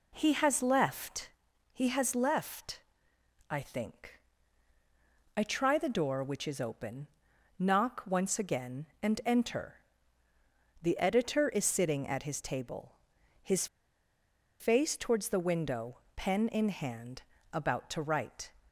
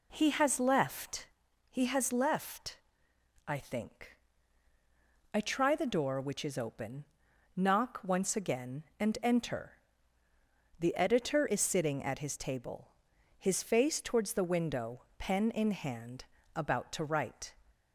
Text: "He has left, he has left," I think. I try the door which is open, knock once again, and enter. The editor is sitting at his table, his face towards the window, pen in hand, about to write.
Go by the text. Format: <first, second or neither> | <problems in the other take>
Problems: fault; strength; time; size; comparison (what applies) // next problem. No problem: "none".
second | pauses between "his" and "face"; noticeable; at 13.6 s; 0.94 s long